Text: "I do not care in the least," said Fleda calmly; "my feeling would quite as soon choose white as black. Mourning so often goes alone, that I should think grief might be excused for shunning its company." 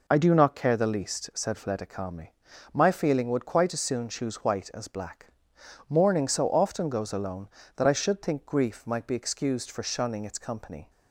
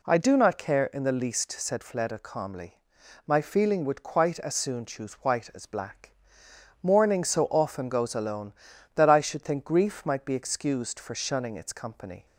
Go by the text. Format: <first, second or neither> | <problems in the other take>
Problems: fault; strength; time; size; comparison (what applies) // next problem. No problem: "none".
second | skips "in"; at 0.7 s